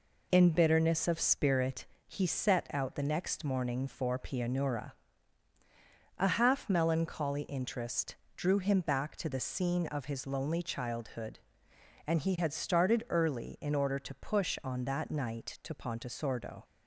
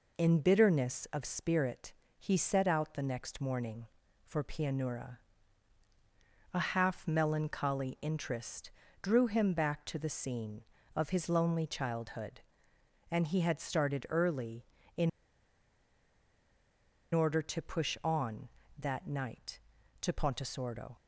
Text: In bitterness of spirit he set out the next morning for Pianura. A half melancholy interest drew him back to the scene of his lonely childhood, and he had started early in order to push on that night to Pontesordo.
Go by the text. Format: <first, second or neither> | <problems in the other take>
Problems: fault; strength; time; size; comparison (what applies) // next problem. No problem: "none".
first | pauses between "spirit" and "he"; slight; at 1.9 s; 0.24 s long; slight in the first // pauses between "interest" and "drew"; slight; at 8.6 s; 0.32 s long; slight in the first // pauses between "in" and "order"; strong; at 15.0 s; 2.0 s long